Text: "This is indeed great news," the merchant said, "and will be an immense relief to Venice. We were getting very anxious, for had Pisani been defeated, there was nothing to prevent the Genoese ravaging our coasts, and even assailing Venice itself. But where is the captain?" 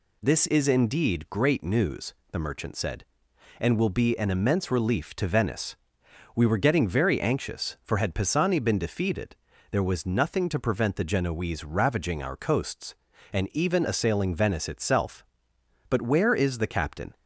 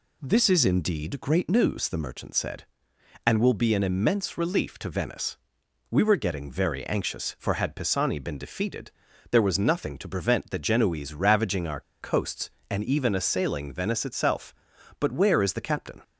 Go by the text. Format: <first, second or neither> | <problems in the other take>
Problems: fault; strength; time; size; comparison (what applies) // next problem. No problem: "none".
first | pauses between "our" and "coasts"; slight; at 11.8 s; 0.20 s long